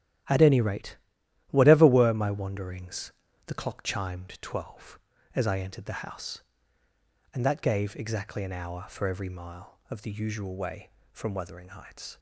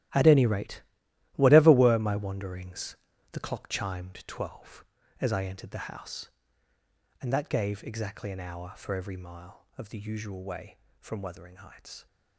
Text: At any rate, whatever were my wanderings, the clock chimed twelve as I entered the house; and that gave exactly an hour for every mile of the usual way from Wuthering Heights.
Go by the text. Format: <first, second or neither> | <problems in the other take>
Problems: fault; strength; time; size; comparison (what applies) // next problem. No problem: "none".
first | gets quieter; strong; throughout; 14 dB // starts louder than the rest; strong; until 1.6 s; 13.5 dB; strong in the first